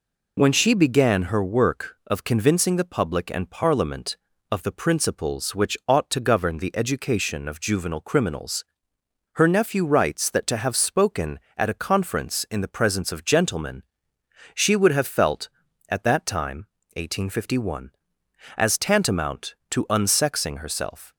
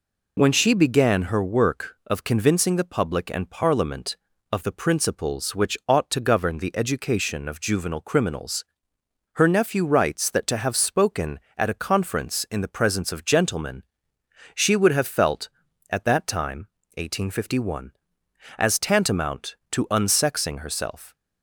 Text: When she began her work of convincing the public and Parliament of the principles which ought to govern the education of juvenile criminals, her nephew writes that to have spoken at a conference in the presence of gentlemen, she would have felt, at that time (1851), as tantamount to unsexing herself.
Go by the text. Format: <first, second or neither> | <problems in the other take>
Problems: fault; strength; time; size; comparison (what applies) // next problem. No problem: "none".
neither | none